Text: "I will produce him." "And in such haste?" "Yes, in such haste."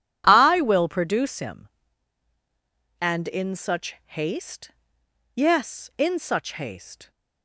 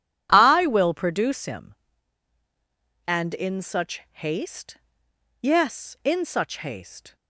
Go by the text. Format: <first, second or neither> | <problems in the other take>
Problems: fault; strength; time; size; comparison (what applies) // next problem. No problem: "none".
neither | none